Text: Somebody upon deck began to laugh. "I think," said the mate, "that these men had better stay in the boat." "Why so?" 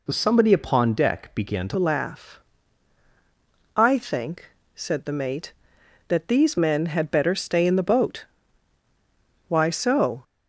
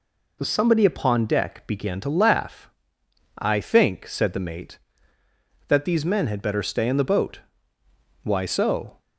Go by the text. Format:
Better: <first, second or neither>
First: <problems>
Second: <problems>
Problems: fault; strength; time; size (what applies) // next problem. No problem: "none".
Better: second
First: changes voice at "laugh"; from 1.7 s on; 8.5 s long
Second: none